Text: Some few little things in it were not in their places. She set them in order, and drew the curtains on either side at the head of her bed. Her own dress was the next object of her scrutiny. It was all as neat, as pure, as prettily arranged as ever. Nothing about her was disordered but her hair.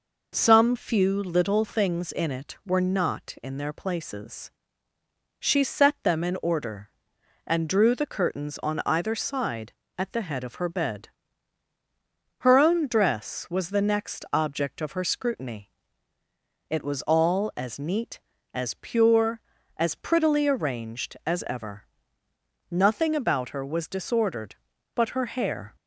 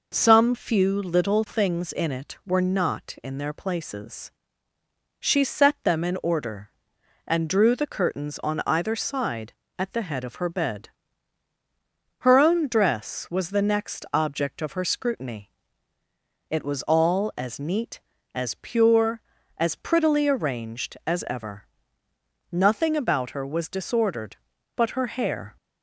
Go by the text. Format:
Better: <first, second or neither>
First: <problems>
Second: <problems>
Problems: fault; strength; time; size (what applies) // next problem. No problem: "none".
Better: neither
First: none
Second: none